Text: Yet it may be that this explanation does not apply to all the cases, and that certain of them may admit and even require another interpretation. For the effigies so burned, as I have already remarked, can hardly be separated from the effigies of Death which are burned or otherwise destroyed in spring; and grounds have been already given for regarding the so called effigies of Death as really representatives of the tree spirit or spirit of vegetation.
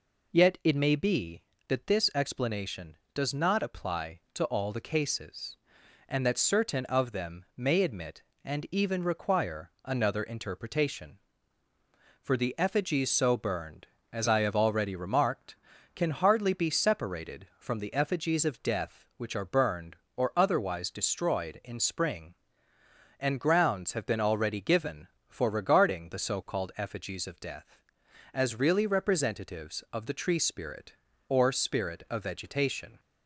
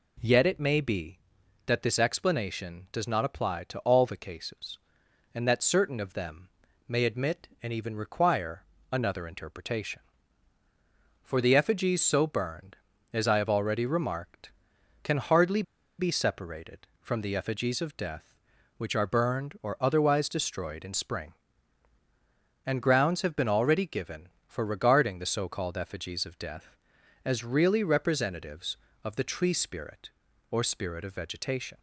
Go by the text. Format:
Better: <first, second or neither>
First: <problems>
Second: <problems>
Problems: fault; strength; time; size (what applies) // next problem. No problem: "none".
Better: first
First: none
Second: pauses between "them" and "may"; at 6.4 s; 0.40 s long // pauses between "require" and "another"; slight; at 8.6 s; 0.28 s long // pauses between "hardly" and "be"; at 15.6 s; 0.36 s long